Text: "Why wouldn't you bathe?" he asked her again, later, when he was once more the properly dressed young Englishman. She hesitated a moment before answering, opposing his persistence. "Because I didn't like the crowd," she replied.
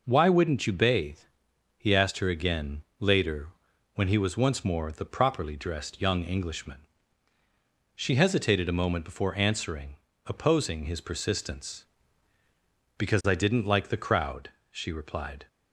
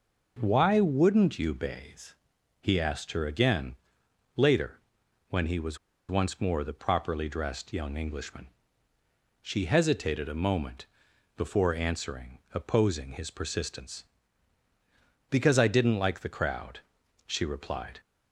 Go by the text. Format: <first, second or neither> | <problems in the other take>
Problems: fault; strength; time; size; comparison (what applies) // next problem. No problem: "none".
first | pauses between "was" and "once"; slight; at 5.7 s; 0.32 s long // pauses between "moment" and "before"; noticeable; at 10.8 s; 0.54 s long